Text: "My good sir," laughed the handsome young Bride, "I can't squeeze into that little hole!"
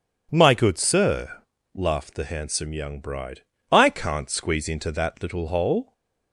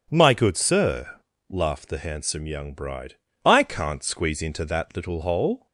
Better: neither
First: none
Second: none

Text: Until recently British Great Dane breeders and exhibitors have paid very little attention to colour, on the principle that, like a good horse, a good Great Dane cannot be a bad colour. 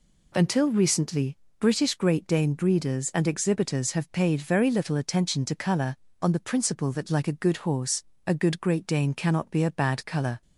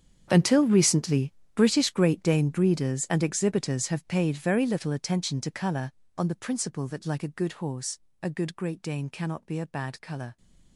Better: first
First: pauses between "recently" and "British"; slight; at 1.3 s; 0.22 s long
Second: gets quieter; strong; throughout; 18 dB // pauses between "recently" and "British"; slight; at 1.3 s; 0.22 s long

